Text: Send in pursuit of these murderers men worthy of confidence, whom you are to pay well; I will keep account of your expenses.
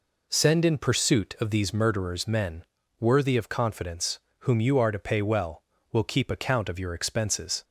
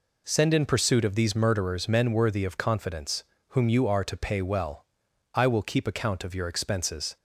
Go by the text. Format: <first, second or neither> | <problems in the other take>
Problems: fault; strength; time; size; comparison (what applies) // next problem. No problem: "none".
second | pauses between "men" and "worthy"; slight; at 2.6 s; 0.36 s long // skips "I"; at 5.7 s